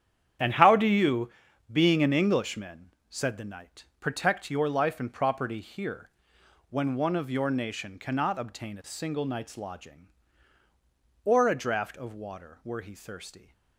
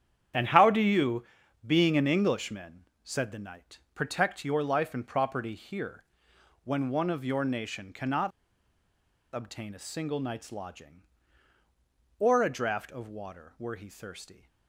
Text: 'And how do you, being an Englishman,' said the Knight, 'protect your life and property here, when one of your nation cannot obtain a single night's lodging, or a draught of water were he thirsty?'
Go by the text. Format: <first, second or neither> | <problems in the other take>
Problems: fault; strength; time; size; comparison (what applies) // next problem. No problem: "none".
first | starts louder than the rest; strong; until 1.7 s; 9 dB; strong in the first // pauses between "cannot" and "obtain"; at 8.3 s; 1.0 s long